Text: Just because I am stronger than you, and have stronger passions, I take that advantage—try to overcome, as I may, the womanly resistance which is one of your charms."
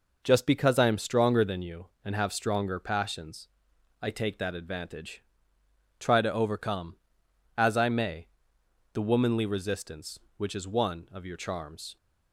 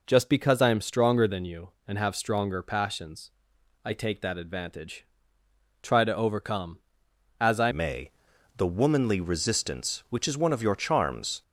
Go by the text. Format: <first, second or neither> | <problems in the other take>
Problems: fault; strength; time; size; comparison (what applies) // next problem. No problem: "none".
first | changes voice at "may"; from 7.7 s on; 3.7 s long